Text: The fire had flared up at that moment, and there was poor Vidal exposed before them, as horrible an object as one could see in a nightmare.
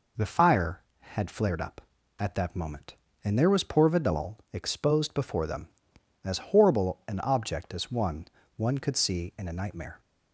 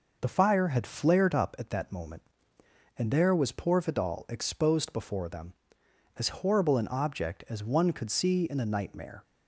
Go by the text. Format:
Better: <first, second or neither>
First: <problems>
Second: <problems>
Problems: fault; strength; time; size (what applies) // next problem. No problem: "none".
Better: second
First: pauses between "Vidal" and "exposed"; slight; at 4.3 s; 0.16 s long // says "one" twice; at 8.5 s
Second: none